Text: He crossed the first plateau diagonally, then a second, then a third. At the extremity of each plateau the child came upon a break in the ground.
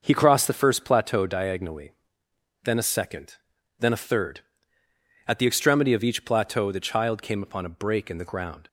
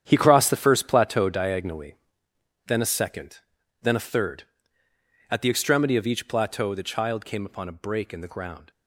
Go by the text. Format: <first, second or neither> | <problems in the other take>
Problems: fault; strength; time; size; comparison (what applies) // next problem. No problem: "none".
first | gets quieter; strong; throughout; 11.5 dB // starts louder than the rest; strong; until 1.0 s; 9 dB; noticeable in the first